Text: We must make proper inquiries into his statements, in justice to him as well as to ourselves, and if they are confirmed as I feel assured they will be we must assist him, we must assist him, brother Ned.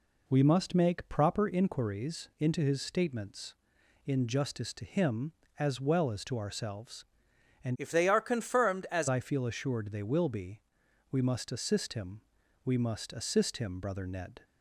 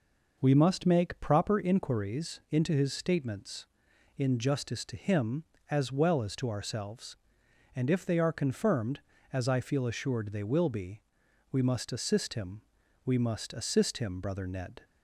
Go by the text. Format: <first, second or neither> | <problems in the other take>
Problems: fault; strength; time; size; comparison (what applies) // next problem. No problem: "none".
second | changes voice from "if" to "as"; from 7.7 to 9.0 s; 1.3 s long // pauses between "be" and "we"; noticeable; at 10.6 s; 0.50 s long; noticeable in the second